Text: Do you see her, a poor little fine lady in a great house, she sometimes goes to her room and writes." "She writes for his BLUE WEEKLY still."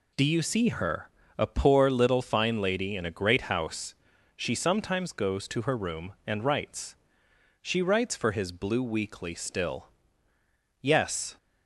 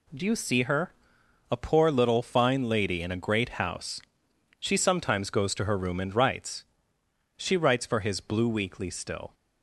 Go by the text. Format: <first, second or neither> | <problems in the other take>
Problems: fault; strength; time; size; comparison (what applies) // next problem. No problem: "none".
second | goes on to say "Yes"; from 10.8 s on; 0.54 s long